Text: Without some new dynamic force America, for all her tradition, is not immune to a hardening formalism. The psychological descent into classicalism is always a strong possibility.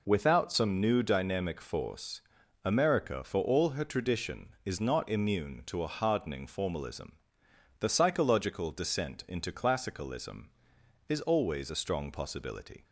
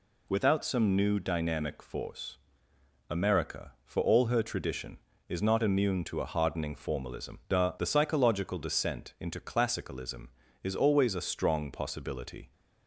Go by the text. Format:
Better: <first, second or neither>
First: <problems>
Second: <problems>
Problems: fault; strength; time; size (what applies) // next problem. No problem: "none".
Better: first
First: pauses between "force" and "America"; at 2.2 s; 0.42 s long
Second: pauses between "force" and "America"; noticeable; at 2.3 s; 0.70 s long // says "The" twice; at 7.7 s